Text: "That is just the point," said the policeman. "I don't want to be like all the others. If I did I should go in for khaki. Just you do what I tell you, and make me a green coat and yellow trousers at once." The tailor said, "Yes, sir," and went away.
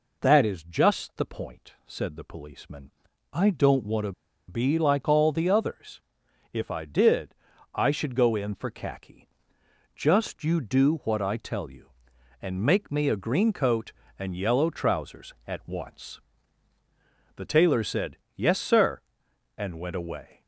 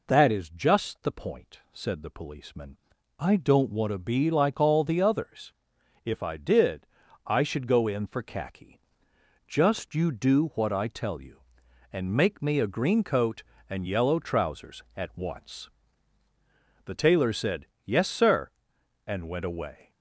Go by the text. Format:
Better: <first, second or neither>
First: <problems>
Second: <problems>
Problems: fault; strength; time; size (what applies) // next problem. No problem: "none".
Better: second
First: pauses between "to" and "be"; at 4.1 s; 0.37 s long // pauses between "did" and "I"; at 7.3 s; 0.42 s long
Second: pauses between "did" and "I"; at 6.8 s; 0.42 s long